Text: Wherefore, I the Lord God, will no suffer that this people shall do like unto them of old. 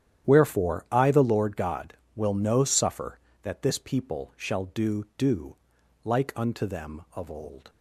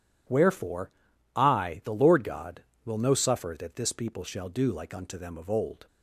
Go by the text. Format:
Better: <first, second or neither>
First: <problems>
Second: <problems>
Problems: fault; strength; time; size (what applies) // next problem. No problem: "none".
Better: second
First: starts louder than the rest; strong; until 1.3 s; 10.5 dB // says "do" twice; at 5.1 s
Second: none